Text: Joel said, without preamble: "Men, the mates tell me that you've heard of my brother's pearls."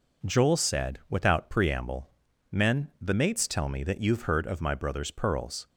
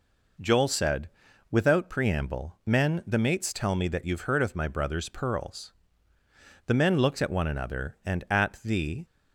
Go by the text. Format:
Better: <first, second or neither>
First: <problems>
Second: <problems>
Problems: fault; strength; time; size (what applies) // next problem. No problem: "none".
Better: first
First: none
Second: goes on to say "The men looked at one another and at the"; strong; from 6.6 s on; 2.3 s long